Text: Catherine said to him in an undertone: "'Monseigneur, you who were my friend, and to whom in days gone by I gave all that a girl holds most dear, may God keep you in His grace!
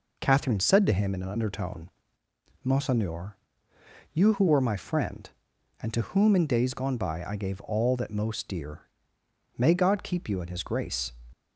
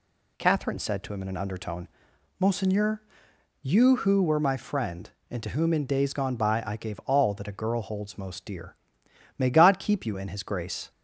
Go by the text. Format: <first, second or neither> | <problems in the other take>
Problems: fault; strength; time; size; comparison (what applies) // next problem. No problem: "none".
second | skips "a girl holds"; at 8.1 s